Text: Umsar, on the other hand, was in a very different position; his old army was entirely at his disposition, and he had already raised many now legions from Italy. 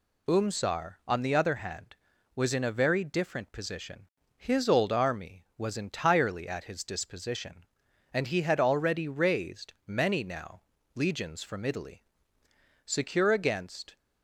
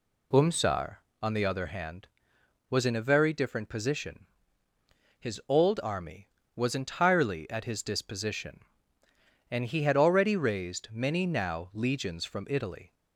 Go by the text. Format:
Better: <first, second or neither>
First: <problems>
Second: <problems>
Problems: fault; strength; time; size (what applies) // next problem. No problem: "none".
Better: second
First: pauses between "now" and "legions"; slight; at 10.6 s; 0.32 s long // goes on to say "Secure against"; noticeable; from 12.8 s on; 1.1 s long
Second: none